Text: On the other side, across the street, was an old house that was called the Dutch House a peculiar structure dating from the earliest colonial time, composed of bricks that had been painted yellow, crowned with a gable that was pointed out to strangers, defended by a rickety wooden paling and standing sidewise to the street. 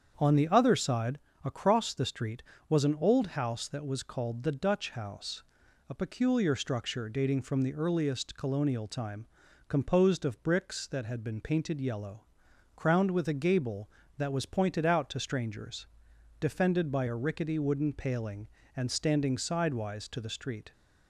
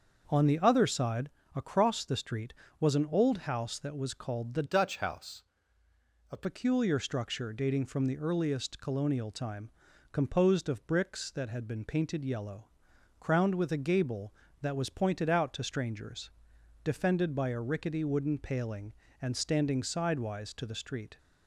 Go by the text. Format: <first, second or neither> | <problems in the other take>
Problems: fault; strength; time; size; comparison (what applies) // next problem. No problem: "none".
first | starts louder than the rest; until 1.2 s; 6.5 dB; strong in the first // changes voice from "Dutch" to "a"; from 4.6 to 6.4 s; 1.8 s long // pauses between "House" and "a"; noticeable; at 5.4 s; 0.86 s long; noticeable in the first